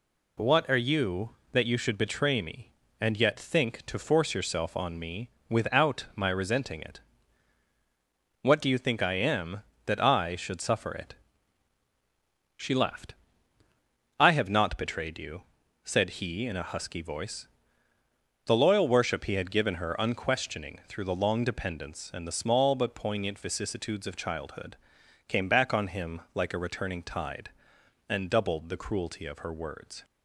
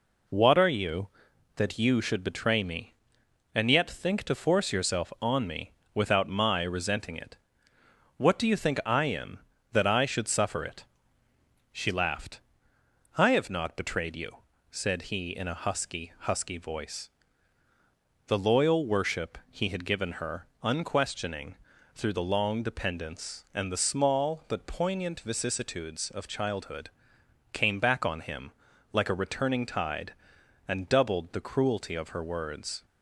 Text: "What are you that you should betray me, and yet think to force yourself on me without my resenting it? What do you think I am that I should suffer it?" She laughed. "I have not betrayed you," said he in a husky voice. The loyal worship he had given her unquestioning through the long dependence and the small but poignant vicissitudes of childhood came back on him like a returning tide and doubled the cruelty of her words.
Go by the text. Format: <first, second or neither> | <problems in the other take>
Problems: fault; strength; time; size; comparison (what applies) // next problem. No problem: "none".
first | pauses between "me" and "without"; slight; at 5.7 s; 0.20 s long; slight in the first // says "husky" twice; at 16.1 s // pauses between "her" and "unquestioning"; slight; at 20.4 s; 0.16 s long // pauses between "unquestioning" and "through"; at 21.5 s; 0.38 s long // pauses between "childhood" and "came"; noticeable; at 26.8 s; 0.64 s long; noticeable in the first // pauses between "him" and "like"; at 28.5 s; 0.40 s long